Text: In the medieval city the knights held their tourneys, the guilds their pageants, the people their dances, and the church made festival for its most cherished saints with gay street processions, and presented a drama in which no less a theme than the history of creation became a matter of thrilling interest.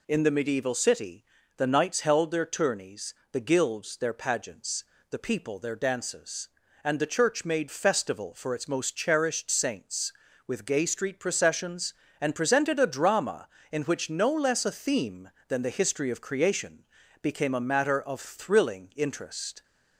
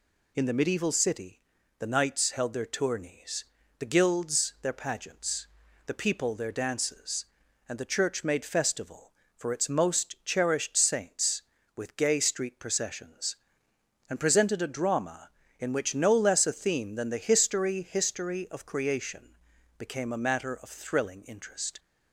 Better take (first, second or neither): first